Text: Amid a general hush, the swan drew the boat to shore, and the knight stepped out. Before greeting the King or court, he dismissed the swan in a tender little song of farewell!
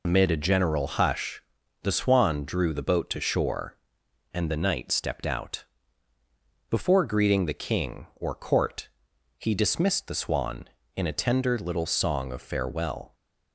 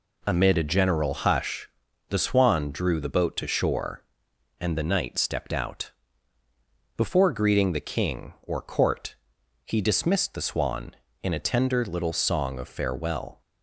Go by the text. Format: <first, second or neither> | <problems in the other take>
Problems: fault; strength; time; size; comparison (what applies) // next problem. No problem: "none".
second | loses the start of "Amid"; at 0.0 s; 80 ms